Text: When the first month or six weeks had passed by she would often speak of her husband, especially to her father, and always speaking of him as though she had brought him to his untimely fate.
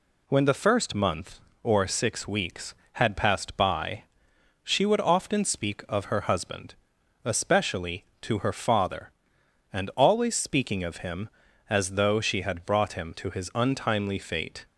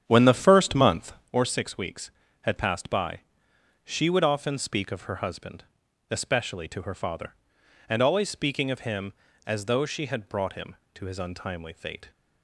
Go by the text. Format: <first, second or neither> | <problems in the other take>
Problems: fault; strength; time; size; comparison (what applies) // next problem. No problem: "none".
first | starts louder than the rest; strong; until 1.3 s; 9 dB // pauses between "by" and "she"; noticeable; at 3.2 s; 0.62 s long; noticeable in the first